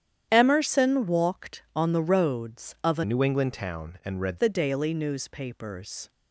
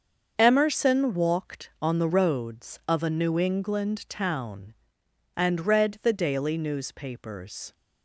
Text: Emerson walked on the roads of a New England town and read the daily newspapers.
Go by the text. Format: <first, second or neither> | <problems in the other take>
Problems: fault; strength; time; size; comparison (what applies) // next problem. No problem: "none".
second | starts louder than the rest; strong; until 1.3 s; 10 dB; also in the second // changes voice from "New" to "read"; from 3.0 to 4.3 s; 1.3 s long